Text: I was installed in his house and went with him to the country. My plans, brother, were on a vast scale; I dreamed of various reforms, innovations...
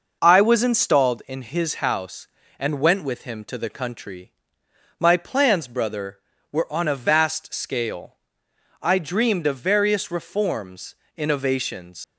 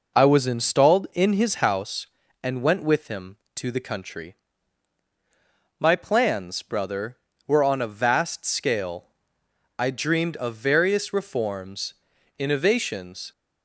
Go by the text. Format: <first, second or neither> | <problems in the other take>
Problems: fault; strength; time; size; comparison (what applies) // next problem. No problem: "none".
second | leaves "innovations" unfinished; at 12.0 s; 110 ms